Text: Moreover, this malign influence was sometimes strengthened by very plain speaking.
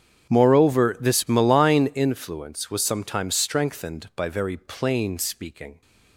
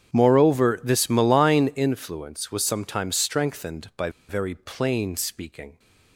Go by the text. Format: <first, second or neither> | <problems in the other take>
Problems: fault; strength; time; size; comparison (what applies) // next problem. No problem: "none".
first | starts louder than the rest; strong; until 1.2 s; 8.5 dB; strong in the first // pauses between "by" and "very"; slight; at 4.0 s; 0.18 s long